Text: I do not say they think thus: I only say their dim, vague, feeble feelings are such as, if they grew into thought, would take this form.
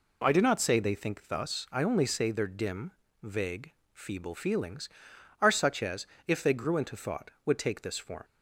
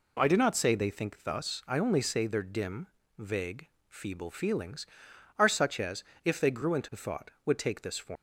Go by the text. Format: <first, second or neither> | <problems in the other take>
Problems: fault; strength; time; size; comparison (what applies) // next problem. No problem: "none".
first | leaves "form" unfinished; at 8.1 s; 90 ms